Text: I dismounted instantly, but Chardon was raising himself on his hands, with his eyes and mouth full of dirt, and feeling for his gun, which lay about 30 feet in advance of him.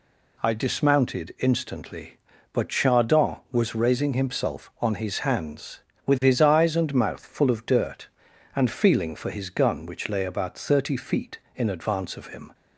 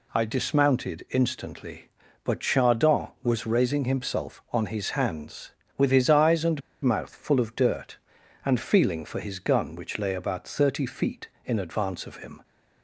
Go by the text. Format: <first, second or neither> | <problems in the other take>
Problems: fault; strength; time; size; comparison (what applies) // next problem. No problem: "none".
first | pauses between "and" and "mouth"; slight; at 6.6 s; 0.22 s long